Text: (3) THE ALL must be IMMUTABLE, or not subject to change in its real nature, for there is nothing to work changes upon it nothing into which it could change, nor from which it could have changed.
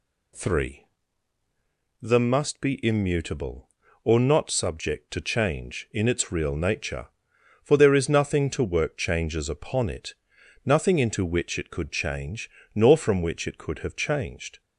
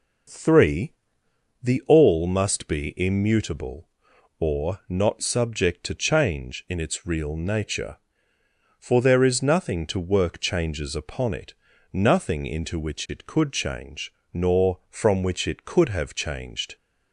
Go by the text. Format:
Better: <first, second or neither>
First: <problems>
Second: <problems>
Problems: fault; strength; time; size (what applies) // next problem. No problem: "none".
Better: second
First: skips "ALL"; at 2.1 s // pauses between "it" and "nothing"; noticeable; at 10.1 s; 0.50 s long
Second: pauses between "it" and "nothing"; at 11.5 s; 0.40 s long